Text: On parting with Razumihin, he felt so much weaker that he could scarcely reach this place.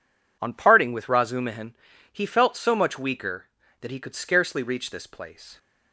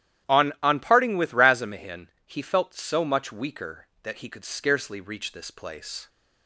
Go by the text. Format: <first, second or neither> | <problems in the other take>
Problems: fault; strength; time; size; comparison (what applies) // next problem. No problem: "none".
first | starts louder than the rest; strong; until 1.3 s; 11.5 dB // says "On" twice; at 0.6 s